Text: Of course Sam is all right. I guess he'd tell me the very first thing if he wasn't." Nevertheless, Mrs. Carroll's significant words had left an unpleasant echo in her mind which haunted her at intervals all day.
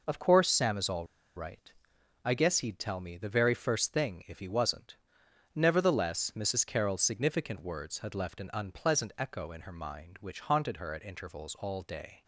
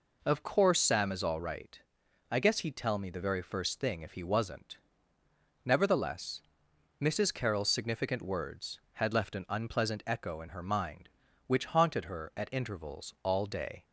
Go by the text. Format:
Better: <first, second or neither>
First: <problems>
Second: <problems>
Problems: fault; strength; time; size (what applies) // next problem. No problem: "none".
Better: second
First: pauses between "all" and "right"; slight; at 1.0 s; 0.30 s long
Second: none